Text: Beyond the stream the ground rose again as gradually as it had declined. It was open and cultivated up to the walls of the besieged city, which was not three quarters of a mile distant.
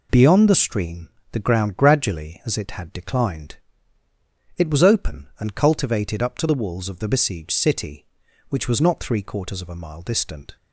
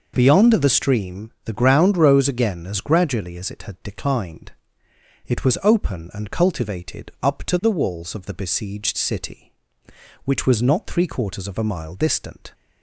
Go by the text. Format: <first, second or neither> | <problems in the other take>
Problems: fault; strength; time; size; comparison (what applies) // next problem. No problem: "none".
second | pauses between "stream" and "the"; slight; at 1.0 s; 0.22 s long // skips "rose again as"; at 1.7 s